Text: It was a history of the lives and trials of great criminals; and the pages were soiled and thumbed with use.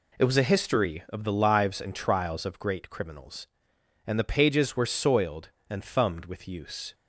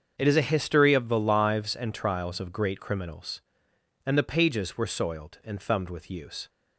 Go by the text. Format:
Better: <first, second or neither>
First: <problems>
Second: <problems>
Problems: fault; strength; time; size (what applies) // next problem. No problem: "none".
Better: first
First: none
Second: starts louder than the rest; until 1.1 s; 7 dB // says "is" for "was"; at 0.2 s